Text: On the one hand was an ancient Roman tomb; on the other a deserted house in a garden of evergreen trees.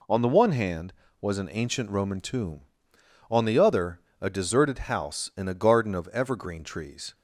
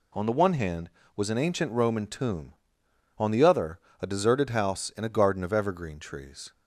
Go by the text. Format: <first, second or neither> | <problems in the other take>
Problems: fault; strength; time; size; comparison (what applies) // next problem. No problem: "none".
neither | pauses between "other" and "a"; slight; the same in both